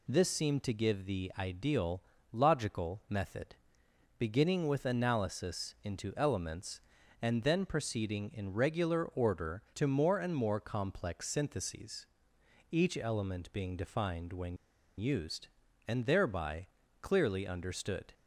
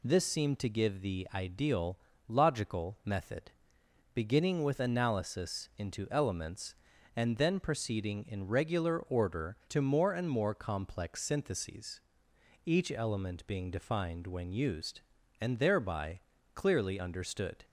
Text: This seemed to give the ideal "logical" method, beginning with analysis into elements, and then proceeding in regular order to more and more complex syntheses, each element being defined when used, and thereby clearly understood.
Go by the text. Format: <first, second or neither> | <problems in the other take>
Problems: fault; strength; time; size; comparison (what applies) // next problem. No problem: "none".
second | pauses between "ideal" and "logical"; slight; at 2.0 s; 0.28 s long; slight in the second // pauses between "when" and "used"; at 14.5 s; 0.42 s long // pauses between "thereby" and "clearly"; slight; at 16.6 s; 0.34 s long; slight in the second